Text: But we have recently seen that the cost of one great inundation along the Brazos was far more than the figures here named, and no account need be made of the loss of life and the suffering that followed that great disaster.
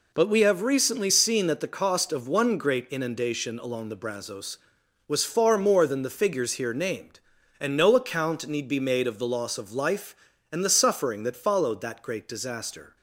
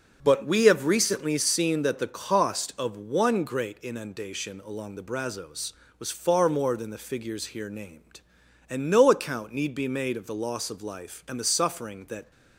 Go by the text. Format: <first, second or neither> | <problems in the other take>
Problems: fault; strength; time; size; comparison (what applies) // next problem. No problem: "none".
first | starts louder than the rest; until 1.2 s; 6.5 dB // stops before "followed that great disaster"; at 12.3 s